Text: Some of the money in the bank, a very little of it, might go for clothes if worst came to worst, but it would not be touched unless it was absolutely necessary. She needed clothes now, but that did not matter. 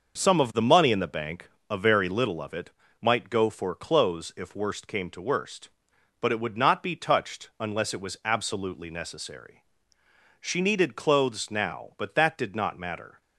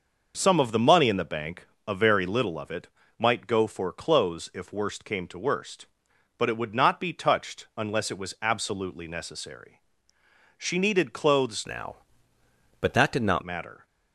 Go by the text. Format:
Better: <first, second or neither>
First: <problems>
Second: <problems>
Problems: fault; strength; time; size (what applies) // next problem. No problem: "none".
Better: first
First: starts louder than the rest; noticeable; until 1.2 s; 6 dB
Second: starts louder than the rest; noticeable; until 1.3 s; 6 dB // changes voice from "now" to "not"; from 11.6 to 13.4 s; 1.8 s long